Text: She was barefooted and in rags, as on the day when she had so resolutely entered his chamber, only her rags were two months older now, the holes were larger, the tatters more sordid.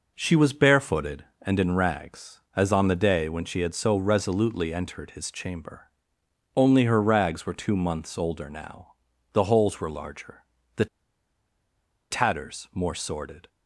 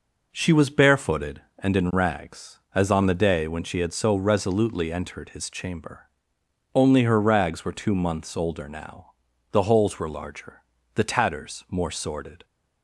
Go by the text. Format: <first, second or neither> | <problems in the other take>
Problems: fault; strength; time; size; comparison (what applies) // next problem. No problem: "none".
second | pauses between "the" and "tatters"; strong; at 10.8 s; 1.2 s long